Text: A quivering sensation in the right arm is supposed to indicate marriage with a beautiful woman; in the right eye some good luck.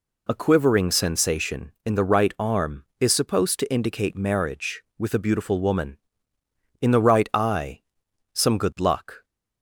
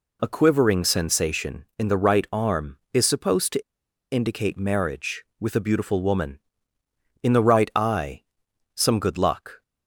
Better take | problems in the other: first | pauses between "to" and "indicate"; noticeable; at 3.6 s; 0.50 s long // pauses between "eye" and "some"; noticeable; at 8.2 s; 0.50 s long; noticeable in the first

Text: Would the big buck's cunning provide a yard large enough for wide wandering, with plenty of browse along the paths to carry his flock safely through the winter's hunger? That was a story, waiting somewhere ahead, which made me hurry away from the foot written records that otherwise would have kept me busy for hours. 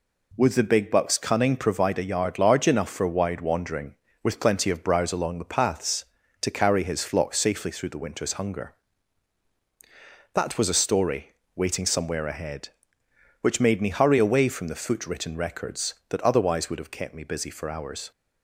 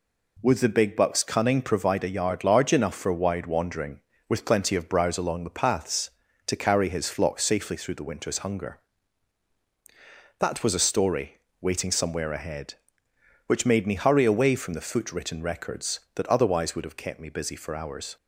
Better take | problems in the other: neither | none

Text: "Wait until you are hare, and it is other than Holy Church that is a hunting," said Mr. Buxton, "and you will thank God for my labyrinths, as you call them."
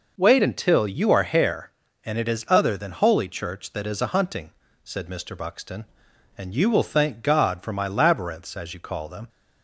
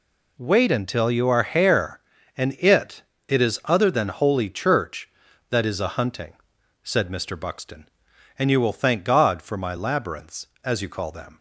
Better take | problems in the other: first | says "it" twice; at 3.2 s

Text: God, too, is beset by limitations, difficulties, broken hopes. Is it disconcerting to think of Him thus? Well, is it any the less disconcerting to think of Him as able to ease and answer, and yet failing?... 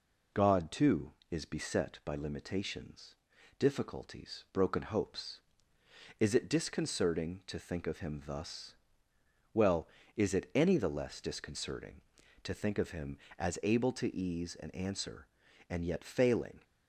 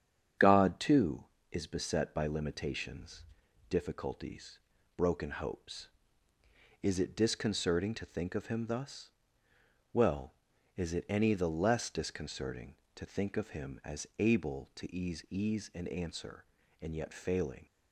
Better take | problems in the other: first | starts louder than the rest; strong; until 1.6 s; 8 dB // says "ease" twice; at 15.3 s

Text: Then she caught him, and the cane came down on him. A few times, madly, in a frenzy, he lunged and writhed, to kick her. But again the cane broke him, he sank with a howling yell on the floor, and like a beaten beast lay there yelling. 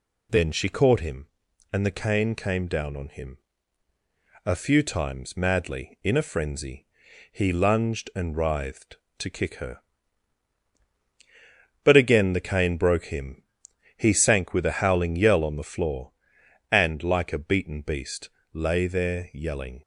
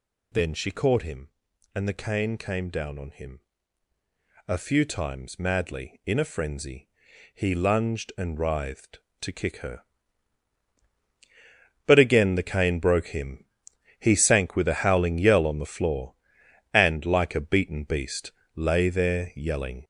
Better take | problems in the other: first | gets louder; noticeable; throughout; 6 dB // pauses between "beast" and "lay"; slight; at 18.3 s; 0.24 s long; slight in the first

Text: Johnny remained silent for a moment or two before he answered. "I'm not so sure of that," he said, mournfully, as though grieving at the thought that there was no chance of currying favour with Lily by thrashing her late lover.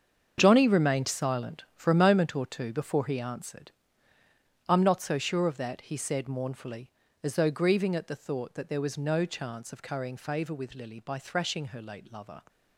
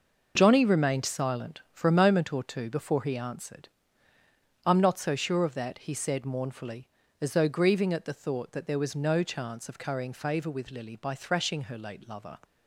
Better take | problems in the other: second | gets quieter; strong; throughout; 11.5 dB

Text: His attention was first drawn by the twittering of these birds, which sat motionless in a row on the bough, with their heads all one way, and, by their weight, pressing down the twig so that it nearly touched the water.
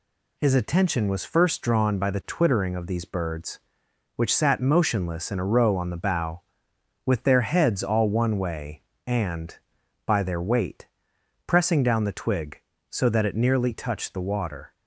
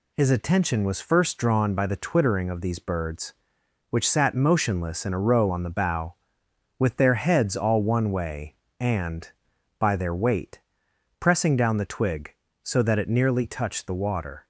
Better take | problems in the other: neither | none

